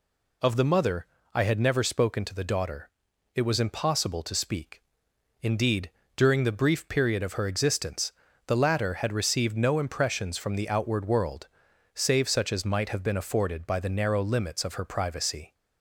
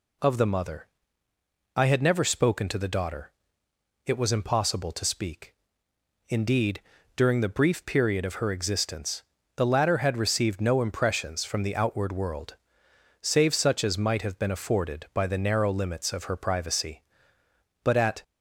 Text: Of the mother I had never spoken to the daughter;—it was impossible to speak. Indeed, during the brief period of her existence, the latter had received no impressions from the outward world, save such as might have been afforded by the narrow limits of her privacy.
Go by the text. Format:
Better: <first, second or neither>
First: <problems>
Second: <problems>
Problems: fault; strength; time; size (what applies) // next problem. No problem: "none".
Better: first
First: pauses between "mother" and "I"; slight; at 1.0 s; 0.28 s long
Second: pauses between "mother" and "I"; noticeable; at 0.8 s; 0.88 s long // goes on to say "But at"; slight; from 17.8 s on; 0.38 s long